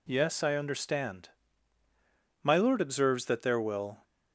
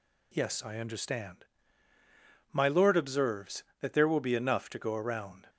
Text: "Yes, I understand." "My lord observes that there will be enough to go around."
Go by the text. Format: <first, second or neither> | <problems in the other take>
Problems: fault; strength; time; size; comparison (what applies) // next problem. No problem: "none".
second | stops before "be enough to go around"; at 4.0 s